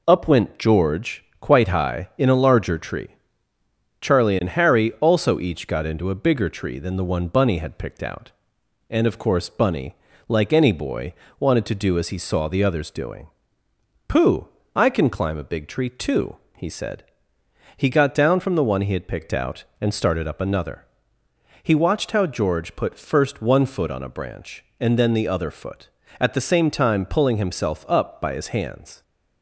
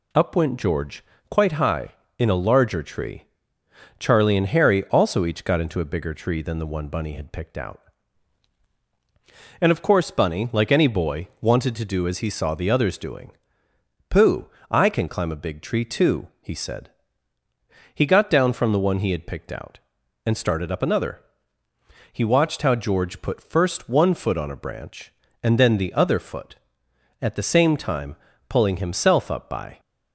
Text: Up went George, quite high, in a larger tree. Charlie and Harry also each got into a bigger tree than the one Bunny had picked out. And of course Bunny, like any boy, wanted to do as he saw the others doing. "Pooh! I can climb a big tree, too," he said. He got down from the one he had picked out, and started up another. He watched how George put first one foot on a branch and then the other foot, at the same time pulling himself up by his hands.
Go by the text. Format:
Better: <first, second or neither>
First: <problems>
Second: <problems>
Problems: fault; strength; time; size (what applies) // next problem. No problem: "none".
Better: first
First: none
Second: pauses between "time" and "pulling"; slight; at 28.1 s; 0.32 s long // stops before "his hands"; at 29.7 s